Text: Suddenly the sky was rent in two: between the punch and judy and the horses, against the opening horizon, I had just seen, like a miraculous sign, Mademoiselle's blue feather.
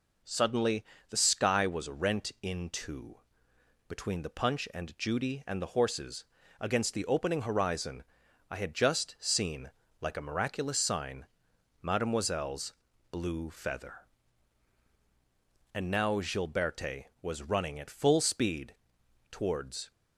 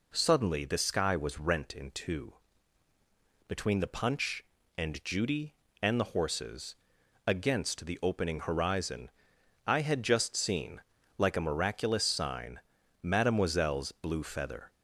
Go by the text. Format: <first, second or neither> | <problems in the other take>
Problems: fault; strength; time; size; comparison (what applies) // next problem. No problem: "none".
second | pauses between "Suddenly" and "the"; slight; at 0.8 s; 0.24 s long // pauses between "Mademoiselle's" and "blue"; at 12.7 s; 0.38 s long // goes on to say "And now Gilberte was running at full speed towards"; strong; from 15.7 s on; 4.1 s long